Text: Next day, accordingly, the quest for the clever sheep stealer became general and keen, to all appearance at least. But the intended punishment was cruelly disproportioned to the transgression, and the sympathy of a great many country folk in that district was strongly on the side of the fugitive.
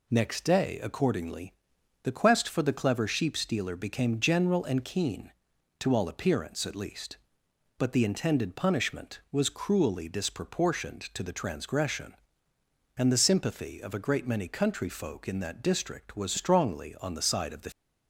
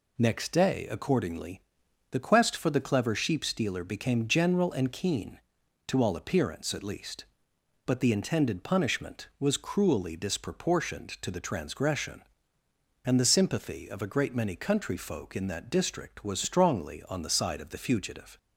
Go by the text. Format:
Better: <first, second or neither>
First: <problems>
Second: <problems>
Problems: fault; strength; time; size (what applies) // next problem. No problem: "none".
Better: second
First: stops before "fugitive"; at 17.7 s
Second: none